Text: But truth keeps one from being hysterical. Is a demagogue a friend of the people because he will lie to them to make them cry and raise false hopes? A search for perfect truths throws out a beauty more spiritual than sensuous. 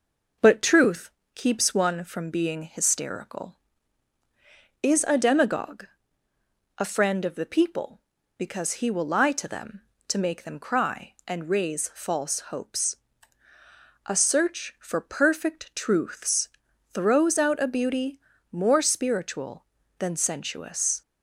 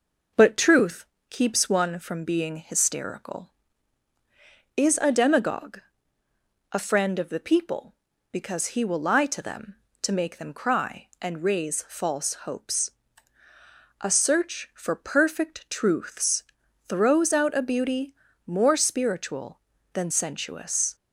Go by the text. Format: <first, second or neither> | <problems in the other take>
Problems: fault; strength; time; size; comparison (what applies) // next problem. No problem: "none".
neither | pauses between "truth" and "keeps"; slight; the same in both // pauses between "demagogue" and "a"; noticeable; the same in both // pauses between "truths" and "throws"; the same in both // pauses between "beauty" and "more"; slight; the same in both